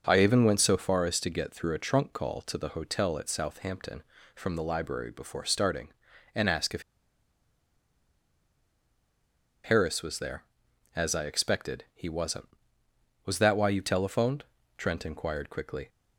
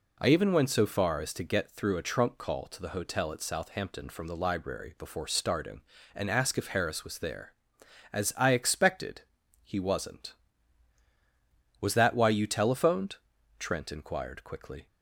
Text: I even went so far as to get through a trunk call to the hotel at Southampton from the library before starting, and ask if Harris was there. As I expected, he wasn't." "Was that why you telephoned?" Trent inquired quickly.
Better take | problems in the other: second | starts louder than the rest; noticeable; until 1.0 s; 6 dB // pauses between "if" and "Harris"; strong; at 6.8 s; 2.8 s long

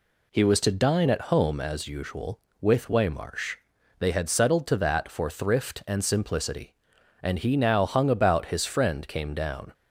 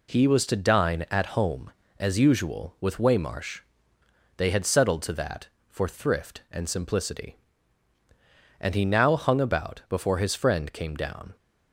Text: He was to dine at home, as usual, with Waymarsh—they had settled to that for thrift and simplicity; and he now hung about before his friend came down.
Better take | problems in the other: second | skips "before"; at 8.4 s

